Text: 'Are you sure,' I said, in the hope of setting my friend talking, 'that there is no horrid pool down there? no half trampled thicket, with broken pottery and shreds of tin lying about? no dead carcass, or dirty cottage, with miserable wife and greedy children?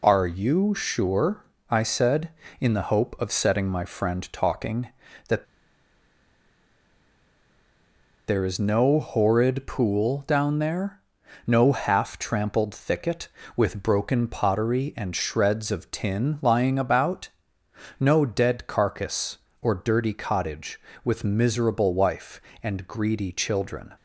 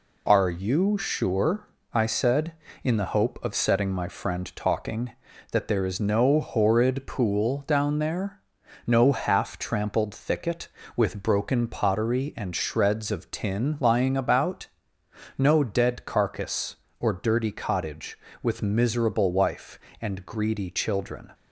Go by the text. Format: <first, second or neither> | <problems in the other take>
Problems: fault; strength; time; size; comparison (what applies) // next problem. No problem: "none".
second | pauses between "that" and "there"; strong; at 5.4 s; 2.8 s long